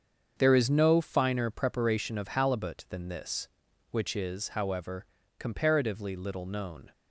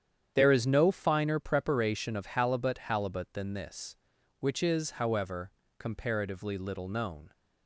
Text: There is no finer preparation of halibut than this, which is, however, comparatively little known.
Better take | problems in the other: first | starts louder than the rest; strong; until 1.3 s; 9 dB; strong in the first // says "halibut" twice; at 2.7 s

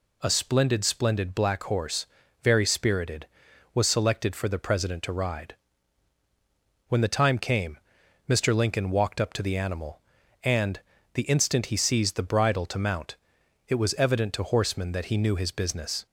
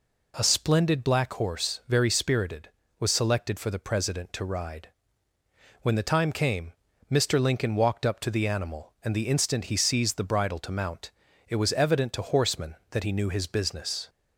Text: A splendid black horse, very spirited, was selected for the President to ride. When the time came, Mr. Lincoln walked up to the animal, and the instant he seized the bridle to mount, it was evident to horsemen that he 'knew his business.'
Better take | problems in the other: second | says "splendid" twice; at 0.8 s // pauses between "and" and "the"; slight; at 10.7 s; 0.34 s long

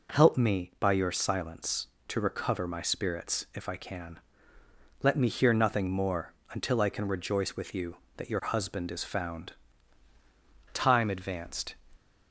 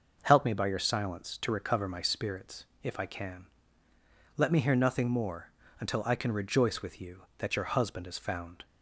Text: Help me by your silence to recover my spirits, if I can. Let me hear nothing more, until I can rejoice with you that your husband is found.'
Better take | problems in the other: second | goes on to say "Time advanced"; noticeable; from 10.7 s on; 1.0 s long

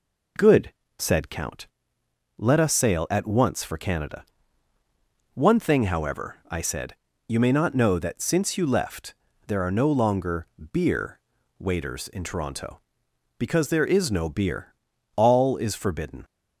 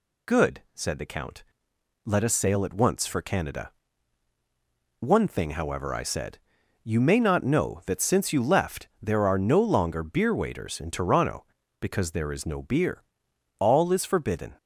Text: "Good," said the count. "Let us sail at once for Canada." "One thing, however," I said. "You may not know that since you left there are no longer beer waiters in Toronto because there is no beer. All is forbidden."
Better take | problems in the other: second | skips "the"; at 1.3 s // pauses between "left" and "there"; slight; at 9.1 s; 0.32 s long // pauses between "longer" and "beer"; slight; at 10.4 s; 0.28 s long // pauses between "beer" and "waiters"; at 11.1 s; 0.38 s long

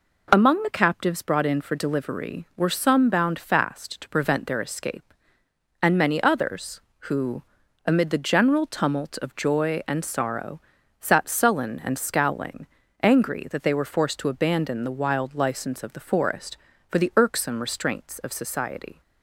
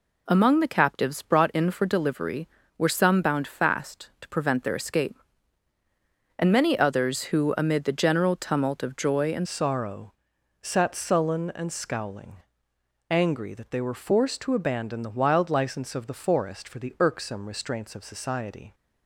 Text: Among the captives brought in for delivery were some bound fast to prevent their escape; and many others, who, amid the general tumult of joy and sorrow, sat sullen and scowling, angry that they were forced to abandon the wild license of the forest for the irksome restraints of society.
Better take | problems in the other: first | changes voice at "sorrow"; from 9.4 s on; 9.3 s long

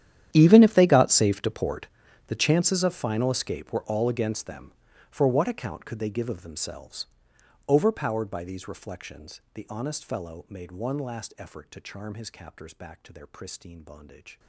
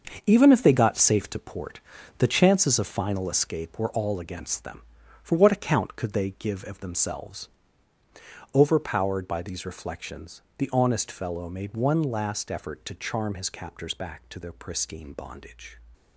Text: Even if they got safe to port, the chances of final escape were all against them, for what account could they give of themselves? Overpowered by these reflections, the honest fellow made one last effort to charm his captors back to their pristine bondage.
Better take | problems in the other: second | gets quieter; strong; throughout; 20.5 dB // starts louder than the rest; strong; until 1.3 s; 11 dB; also in the second

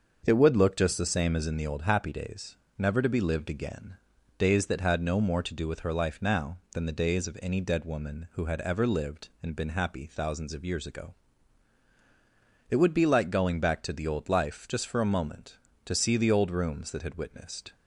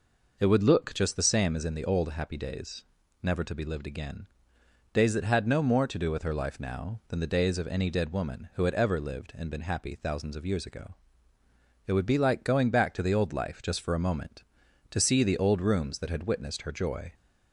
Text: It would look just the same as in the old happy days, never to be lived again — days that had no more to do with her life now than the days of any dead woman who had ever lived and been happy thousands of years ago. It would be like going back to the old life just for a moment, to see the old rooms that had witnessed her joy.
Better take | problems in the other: second | starts louder than the rest; until 1.2 s; 6.5 dB // stops before "her joy"; at 17.7 s

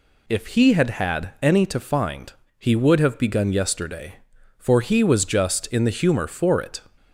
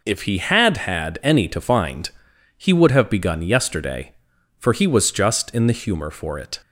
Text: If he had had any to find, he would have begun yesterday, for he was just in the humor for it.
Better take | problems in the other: neither | none

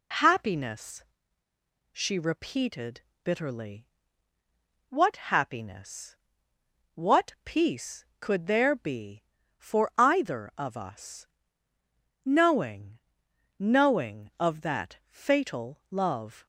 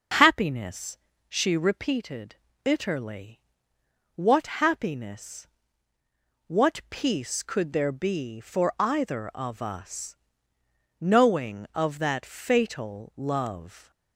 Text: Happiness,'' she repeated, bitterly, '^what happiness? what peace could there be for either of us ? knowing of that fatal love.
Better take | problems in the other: second | says "knowing" twice; at 13.5 s

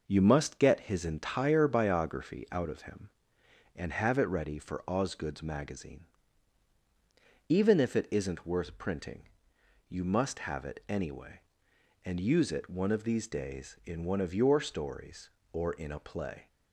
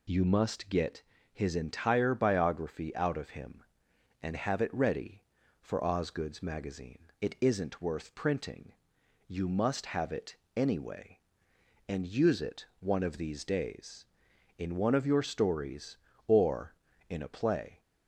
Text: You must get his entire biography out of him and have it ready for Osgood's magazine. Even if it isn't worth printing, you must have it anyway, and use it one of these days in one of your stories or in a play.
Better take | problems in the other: first | pauses between "get" and "his"; slight; at 1.0 s; 0.32 s long // skips "Even if"; at 7.1 s // pauses between "it" and "anyway"; slight; at 10.3 s; 0.20 s long // pauses between "it" and "one"; slight; at 12.6 s; 0.16 s long

